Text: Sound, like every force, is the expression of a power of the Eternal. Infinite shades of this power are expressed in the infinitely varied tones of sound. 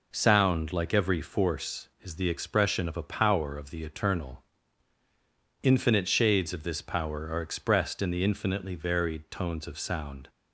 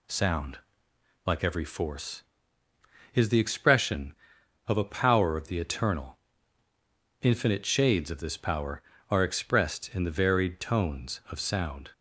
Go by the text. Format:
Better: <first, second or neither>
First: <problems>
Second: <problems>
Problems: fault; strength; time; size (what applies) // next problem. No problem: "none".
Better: first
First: none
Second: skips "infinitely"; at 10.1 s